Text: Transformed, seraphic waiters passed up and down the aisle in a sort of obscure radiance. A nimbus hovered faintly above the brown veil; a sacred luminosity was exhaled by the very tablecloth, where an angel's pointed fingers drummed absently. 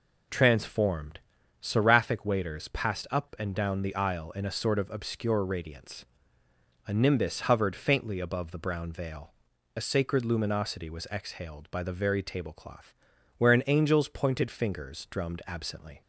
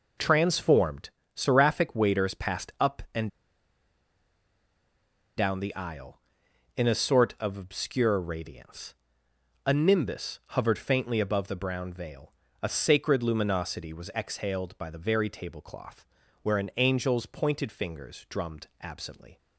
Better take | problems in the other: first | pauses between "and" and "down"; strong; at 3.2 s; 2.0 s long

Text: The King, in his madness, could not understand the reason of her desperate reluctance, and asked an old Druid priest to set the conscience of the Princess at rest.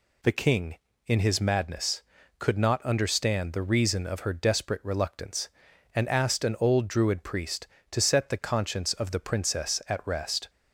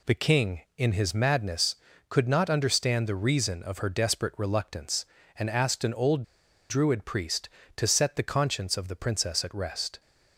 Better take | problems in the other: first | pauses between "old" and "Druid"; noticeable; at 6.2 s; 0.47 s long

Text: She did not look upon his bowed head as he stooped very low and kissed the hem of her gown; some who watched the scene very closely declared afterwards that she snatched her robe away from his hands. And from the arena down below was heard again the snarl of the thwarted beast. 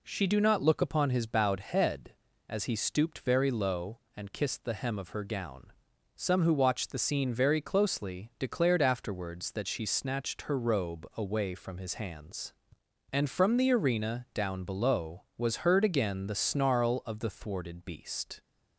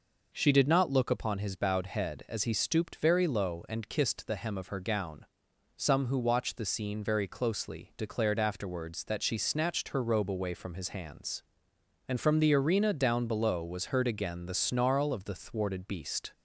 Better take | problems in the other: second | says "do" for "did"; at 0.2 s

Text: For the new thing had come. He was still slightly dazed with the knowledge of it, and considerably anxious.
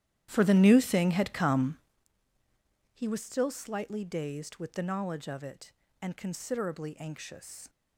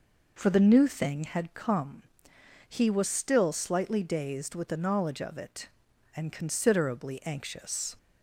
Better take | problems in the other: second | starts louder than the rest; strong; until 2.1 s; 11.5 dB

